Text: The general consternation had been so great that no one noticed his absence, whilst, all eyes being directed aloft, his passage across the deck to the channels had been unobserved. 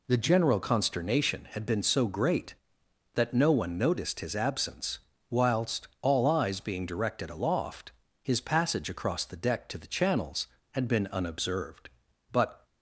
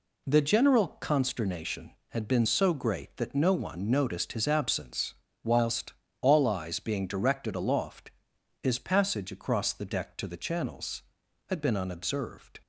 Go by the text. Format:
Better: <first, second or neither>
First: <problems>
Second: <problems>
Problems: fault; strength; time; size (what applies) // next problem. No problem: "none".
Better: second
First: goes on to say "But"; slight; from 12.3 s on; 0.34 s long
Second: none